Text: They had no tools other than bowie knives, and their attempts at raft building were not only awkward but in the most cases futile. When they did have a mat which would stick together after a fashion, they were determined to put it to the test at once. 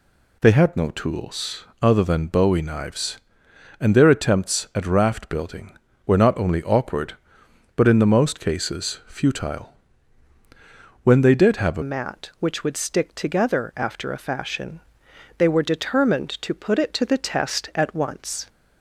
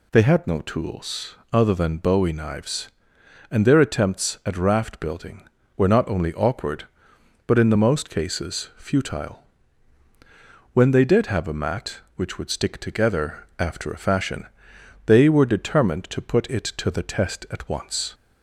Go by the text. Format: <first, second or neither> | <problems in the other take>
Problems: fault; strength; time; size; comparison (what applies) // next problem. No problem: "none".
second | pauses between "tools" and "other"; slight; at 1.6 s; 0.18 s long; slight in the second // changes voice at "mat"; from 11.8 s on; 6.6 s long